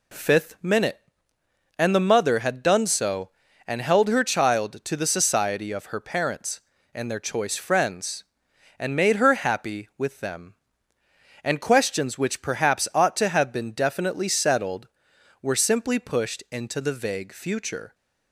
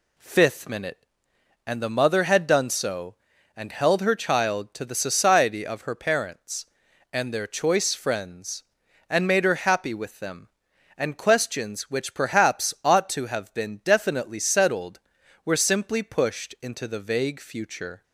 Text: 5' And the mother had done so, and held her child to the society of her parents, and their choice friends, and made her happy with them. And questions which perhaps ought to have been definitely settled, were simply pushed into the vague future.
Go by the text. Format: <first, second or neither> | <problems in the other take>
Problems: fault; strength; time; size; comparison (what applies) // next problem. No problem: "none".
neither | none